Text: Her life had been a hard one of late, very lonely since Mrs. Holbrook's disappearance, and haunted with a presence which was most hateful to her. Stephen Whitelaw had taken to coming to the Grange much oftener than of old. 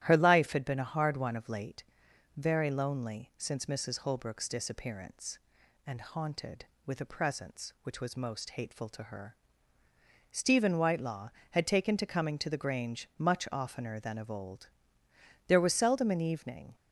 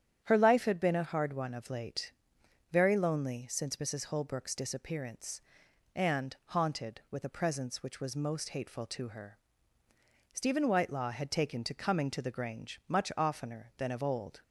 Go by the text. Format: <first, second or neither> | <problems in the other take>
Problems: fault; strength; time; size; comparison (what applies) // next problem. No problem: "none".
second | starts louder than the rest; strong; until 1.0 s; 13 dB; strong in the second // goes on to say "There was seldom an evening"; noticeable; from 15.4 s on; 1.2 s long